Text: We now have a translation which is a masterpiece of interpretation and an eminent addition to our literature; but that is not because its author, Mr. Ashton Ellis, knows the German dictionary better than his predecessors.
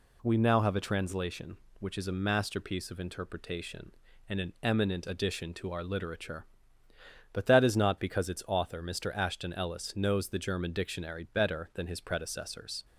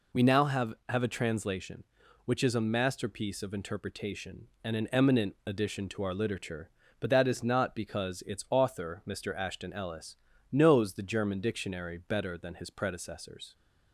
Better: first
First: none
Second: says "have" twice; at 0.8 s

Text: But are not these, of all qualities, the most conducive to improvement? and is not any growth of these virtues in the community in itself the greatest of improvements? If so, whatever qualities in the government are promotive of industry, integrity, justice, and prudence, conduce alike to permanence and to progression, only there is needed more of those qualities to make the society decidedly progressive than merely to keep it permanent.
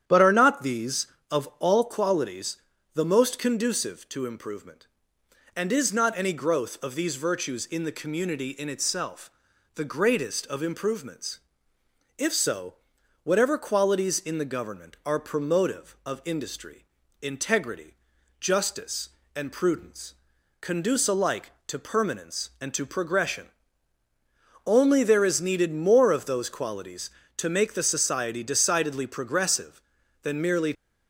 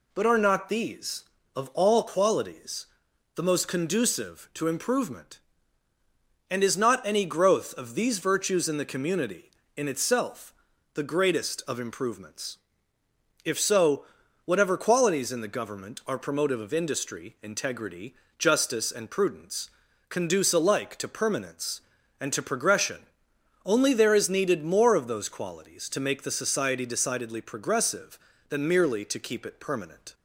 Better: second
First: starts louder than the rest; strong; until 1.0 s; 9.5 dB // pauses between "itself" and "the"; noticeable; at 9.3 s; 0.46 s long // stops before "to keep it permanent"; at 30.7 s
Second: pauses between "itself" and "the"; at 10.5 s; 0.44 s long

